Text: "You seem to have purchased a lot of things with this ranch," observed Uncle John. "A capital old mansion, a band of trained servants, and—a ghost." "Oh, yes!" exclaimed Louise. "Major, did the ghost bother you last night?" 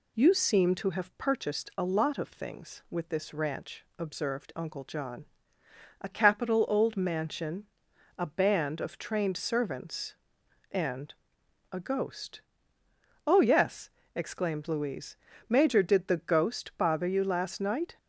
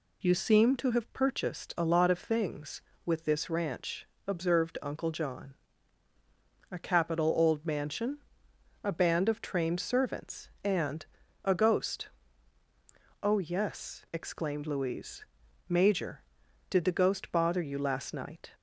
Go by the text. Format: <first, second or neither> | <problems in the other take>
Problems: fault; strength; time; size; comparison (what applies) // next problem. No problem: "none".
neither | none